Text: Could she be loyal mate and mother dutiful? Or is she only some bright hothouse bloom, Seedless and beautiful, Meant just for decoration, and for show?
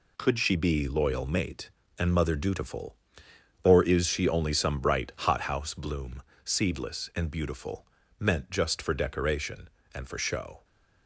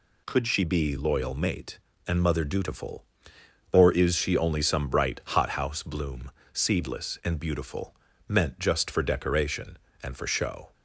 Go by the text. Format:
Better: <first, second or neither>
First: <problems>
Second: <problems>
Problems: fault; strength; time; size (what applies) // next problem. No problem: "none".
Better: second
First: gets quieter; strong; throughout; 8 dB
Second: none